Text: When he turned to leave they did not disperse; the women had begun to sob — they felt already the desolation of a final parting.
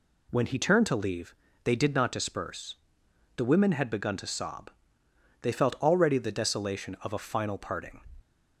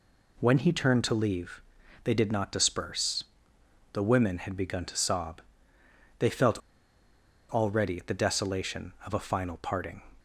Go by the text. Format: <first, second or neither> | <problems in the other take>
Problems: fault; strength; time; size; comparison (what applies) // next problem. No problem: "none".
first | pauses between "leave" and "they"; at 1.6 s; 0.40 s long; slight in the first // pauses between "felt" and "already"; noticeable; at 6.5 s; 0.90 s long